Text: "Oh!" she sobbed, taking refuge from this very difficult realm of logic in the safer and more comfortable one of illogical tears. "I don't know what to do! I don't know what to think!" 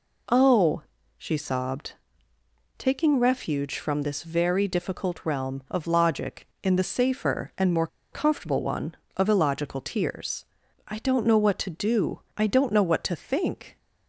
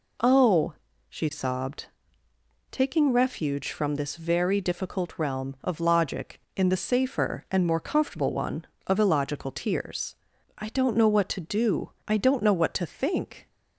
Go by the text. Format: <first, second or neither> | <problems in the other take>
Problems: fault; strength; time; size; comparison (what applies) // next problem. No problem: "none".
second | pauses between "more" and "comfortable"; slight; at 7.8 s; 0.25 s long